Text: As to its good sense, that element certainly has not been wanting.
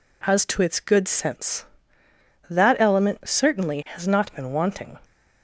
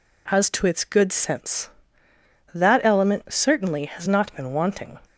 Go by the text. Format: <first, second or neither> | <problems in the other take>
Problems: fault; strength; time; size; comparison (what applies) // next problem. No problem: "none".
neither | none